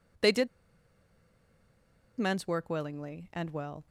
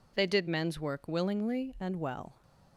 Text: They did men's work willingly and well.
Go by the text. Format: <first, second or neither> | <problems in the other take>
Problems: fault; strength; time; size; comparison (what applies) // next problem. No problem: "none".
second | pauses between "did" and "men's"; strong; at 0.4 s; 1.7 s long